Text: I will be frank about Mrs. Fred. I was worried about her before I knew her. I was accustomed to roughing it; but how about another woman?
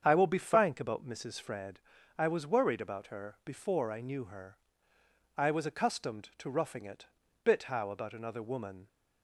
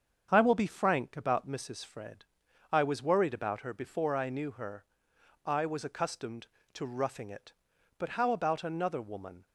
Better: second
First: starts louder than the rest; strong; until 1.0 s; 7.5 dB // says "bit" for "but"; at 7.4 s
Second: starts louder than the rest; strong; until 1.3 s; 7.5 dB

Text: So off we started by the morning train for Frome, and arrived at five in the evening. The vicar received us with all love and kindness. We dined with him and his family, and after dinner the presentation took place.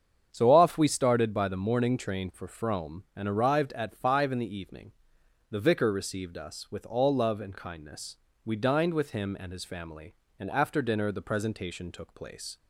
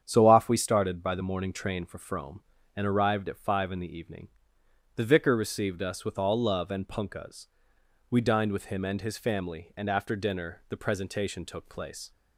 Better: first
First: starts louder than the rest; strong; until 1.3 s; 8 dB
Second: starts louder than the rest; strong; until 1.0 s; 8.5 dB // says "punkahs" for "kindness"; at 6.8 s

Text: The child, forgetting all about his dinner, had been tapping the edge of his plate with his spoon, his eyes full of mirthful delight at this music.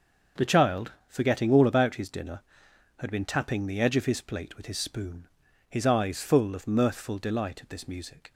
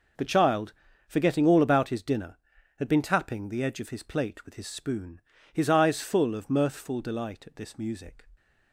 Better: neither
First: none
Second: none

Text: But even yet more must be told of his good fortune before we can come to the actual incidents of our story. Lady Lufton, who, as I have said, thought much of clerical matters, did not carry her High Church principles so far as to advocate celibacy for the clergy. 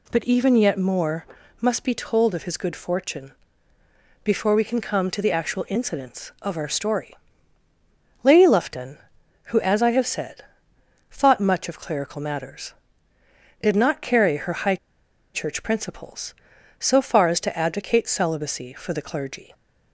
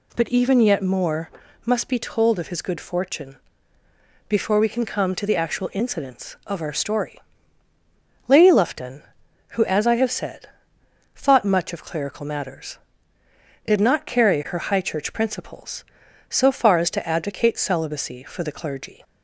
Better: second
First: pauses between "more" and "must"; slight; at 1.2 s; 0.34 s long // pauses between "fortune" and "before"; noticeable; at 3.3 s; 0.90 s long // pauses between "High" and "Church"; noticeable; at 14.7 s; 0.58 s long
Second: pauses between "more" and "must"; slight; at 1.3 s; 0.34 s long // pauses between "fortune" and "before"; noticeable; at 3.3 s; 0.90 s long

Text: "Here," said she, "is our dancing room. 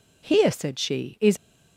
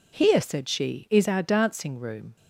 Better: second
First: stops before "our dancing room"; at 1.3 s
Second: none

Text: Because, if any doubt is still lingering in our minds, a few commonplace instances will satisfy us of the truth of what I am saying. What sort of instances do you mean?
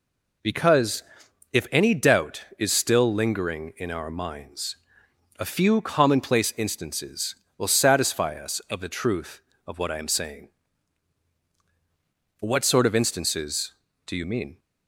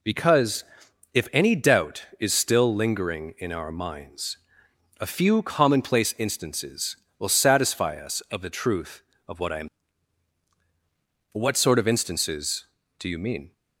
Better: first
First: none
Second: skips "saying"; at 10.5 s

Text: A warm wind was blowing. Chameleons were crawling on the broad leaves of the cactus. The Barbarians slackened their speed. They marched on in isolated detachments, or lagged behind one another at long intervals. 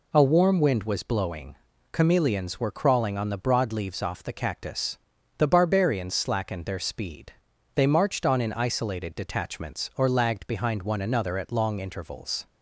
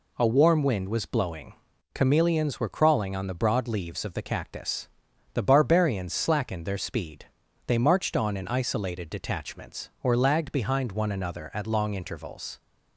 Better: second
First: says "off" for "of"; at 4.0 s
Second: none

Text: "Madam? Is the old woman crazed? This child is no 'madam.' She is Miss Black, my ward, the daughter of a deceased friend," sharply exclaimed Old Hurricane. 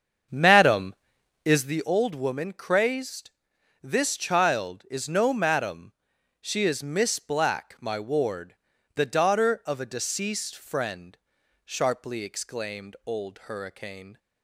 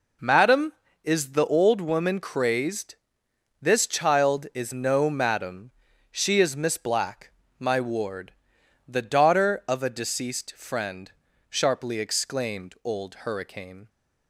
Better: second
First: starts louder than the rest; strong; until 1.8 s; 7 dB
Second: none

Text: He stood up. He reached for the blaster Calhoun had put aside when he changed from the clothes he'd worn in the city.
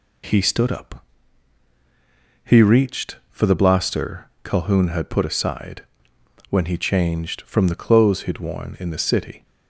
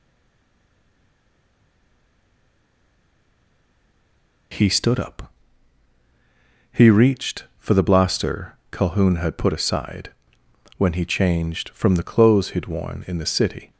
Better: first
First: pauses between "blaster" and "Calhoun"; slight; at 4.2 s; 0.16 s long // pauses between "aside" and "when"; noticeable; at 5.8 s; 0.66 s long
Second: stays silent before the first word; strong; until 4.5 s; 4.5 s long // pauses between "blaster" and "Calhoun"; slight; at 8.5 s; 0.16 s long // pauses between "aside" and "when"; noticeable; at 10.1 s; 0.66 s long

